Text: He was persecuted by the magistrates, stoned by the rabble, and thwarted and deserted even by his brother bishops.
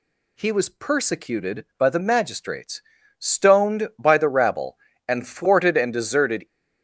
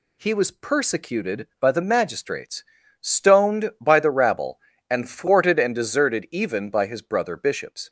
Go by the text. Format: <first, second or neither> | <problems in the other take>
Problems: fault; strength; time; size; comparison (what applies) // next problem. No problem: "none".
second | stops before "even by his brother bishops"; at 6.4 s